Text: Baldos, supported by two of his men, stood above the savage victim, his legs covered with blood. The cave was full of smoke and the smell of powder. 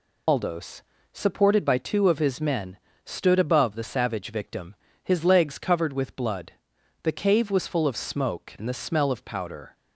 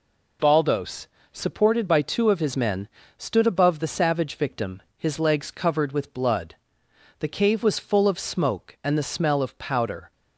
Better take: second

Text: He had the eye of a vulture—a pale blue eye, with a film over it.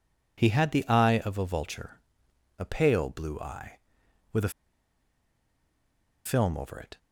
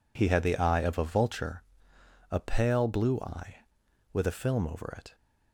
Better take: second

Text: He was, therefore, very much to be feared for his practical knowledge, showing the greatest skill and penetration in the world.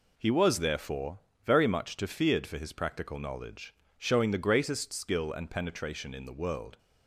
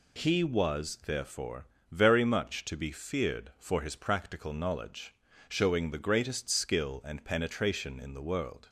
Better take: second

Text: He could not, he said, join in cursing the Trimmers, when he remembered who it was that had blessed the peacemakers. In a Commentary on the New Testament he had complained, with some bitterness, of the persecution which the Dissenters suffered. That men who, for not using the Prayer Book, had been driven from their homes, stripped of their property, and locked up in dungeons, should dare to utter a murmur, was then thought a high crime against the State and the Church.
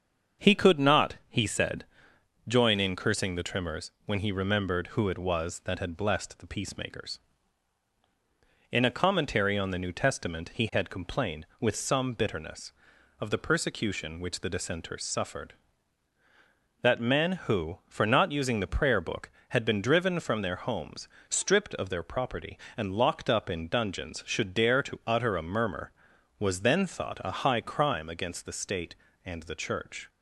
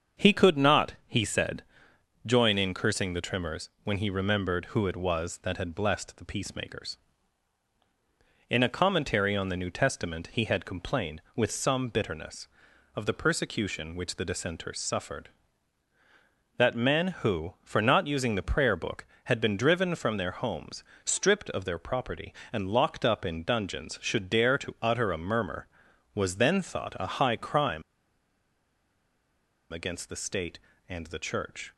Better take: first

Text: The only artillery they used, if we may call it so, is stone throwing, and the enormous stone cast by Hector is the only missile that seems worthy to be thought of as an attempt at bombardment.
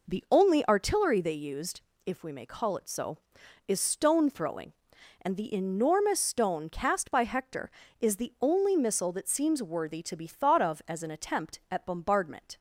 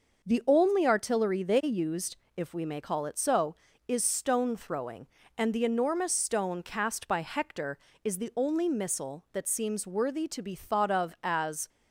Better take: first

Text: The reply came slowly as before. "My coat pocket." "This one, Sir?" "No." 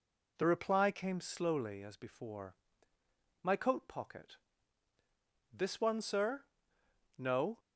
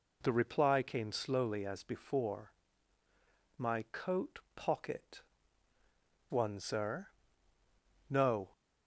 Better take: first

